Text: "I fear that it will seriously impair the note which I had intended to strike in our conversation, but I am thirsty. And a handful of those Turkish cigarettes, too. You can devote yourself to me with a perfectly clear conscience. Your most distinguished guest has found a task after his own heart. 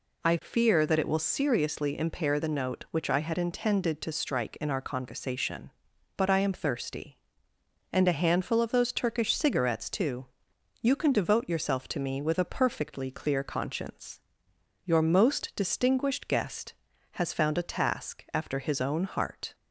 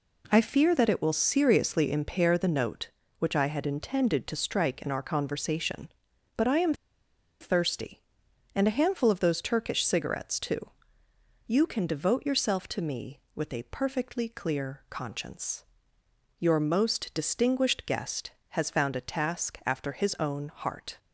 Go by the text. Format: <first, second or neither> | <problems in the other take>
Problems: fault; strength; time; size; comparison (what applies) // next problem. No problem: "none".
first | pauses between "am" and "thirsty"; noticeable; at 6.7 s; 0.66 s long